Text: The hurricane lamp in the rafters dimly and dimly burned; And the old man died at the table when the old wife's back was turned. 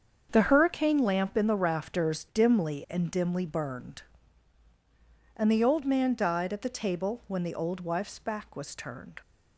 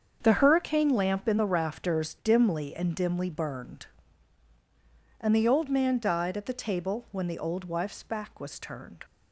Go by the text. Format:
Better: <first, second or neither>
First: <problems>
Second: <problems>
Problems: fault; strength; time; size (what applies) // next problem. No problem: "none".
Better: neither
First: starts louder than the rest; until 1.3 s; 7 dB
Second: starts louder than the rest; until 1.2 s; 7 dB